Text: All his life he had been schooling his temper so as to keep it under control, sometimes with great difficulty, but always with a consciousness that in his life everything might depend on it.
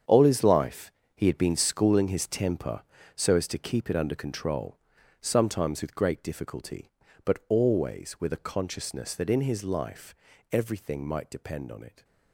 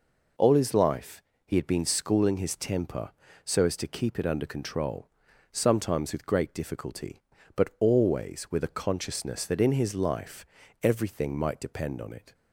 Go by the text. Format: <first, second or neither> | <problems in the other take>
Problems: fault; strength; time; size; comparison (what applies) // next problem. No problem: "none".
second | gets quieter; strong; throughout; 11.5 dB // pauses between "life" and "he"; slight; at 0.9 s; 0.24 s long; slight in the second // pauses between "life" and "everything"; at 10.1 s; 0.38 s long; also in the second